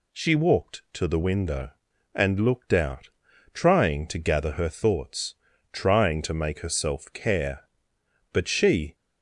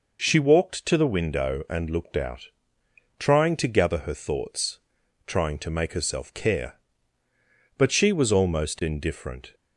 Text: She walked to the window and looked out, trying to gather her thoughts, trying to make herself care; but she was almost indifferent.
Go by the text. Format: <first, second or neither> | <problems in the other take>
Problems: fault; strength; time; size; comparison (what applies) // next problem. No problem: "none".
second | stops before "was almost indifferent"; at 8.9 s